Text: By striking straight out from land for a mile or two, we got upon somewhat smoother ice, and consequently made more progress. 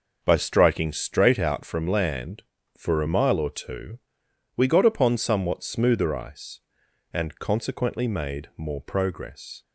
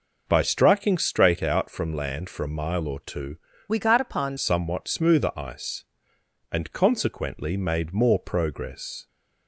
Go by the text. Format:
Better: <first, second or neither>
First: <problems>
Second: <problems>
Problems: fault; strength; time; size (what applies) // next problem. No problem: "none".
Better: first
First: none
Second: changes voice from "we" to "upon"; from 3.6 to 4.3 s; 0.7 s long